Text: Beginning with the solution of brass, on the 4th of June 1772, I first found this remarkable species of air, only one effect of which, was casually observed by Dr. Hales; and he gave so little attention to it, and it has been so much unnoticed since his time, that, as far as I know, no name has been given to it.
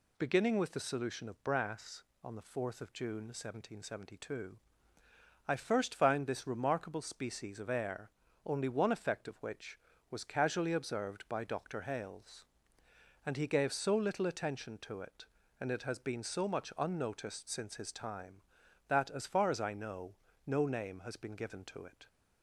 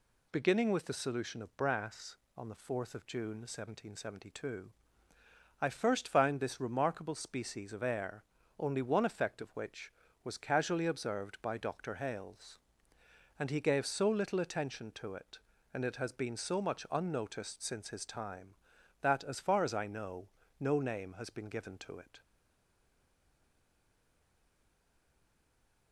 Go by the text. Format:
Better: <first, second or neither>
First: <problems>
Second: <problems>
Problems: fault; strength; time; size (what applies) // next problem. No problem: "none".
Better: first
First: none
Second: stays silent after the last word; strong; from 22.2 s on; 3.7 s long